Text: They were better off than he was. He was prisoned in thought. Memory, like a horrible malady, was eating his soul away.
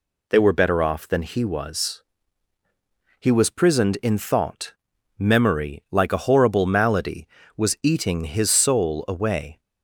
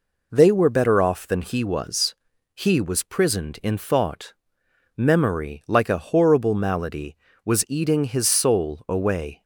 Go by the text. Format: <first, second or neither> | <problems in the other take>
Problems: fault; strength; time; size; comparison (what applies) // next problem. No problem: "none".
neither | none